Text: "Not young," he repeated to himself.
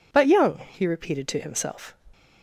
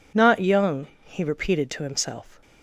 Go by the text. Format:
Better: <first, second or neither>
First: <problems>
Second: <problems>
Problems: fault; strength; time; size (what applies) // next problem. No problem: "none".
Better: second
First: says "But" for "Not"; at 0.1 s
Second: none